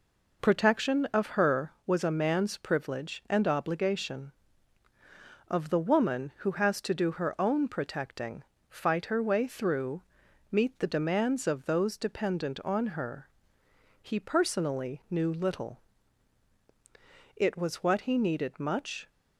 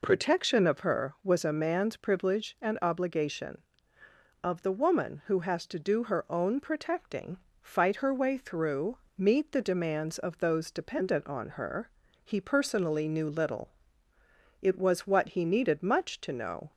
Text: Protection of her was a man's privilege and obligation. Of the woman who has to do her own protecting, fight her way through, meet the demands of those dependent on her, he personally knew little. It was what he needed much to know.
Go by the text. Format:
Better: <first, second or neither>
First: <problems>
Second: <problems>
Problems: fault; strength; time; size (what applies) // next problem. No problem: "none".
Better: second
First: stops before "to know"; at 19.0 s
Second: none